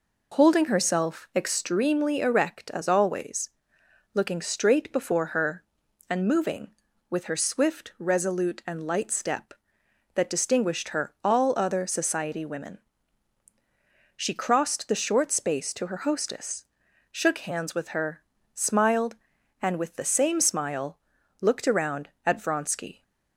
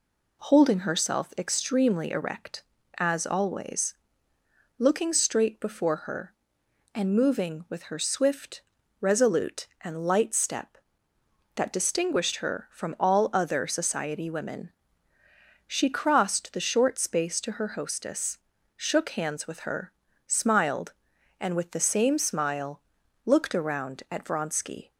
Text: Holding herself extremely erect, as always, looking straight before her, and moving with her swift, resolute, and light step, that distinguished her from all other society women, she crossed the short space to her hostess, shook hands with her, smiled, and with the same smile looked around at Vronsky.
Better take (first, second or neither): second